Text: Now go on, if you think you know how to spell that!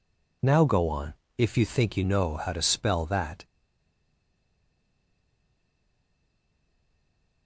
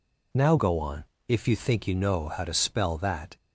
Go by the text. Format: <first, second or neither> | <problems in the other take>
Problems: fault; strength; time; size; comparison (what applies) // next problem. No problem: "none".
second | stays silent after the last word; strong; from 3.4 s on; 4.0 s long